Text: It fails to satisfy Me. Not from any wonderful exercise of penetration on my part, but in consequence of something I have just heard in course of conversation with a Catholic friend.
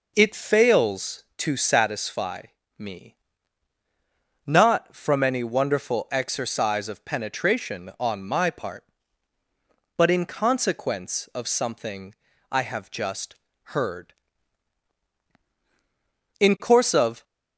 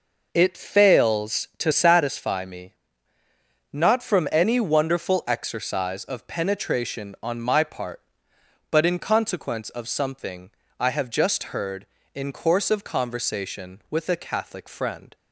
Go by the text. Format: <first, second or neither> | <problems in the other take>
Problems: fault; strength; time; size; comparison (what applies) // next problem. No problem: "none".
second | pauses between "satisfy" and "Me"; slight; at 2.4 s; 0.36 s long // pauses between "something" and "I"; slight; at 12.1 s; 0.34 s long; slight in the second // pauses between "just" and "heard"; slight; at 13.3 s; 0.30 s long // stops before "conversation with a Catholic friend"; at 17.2 s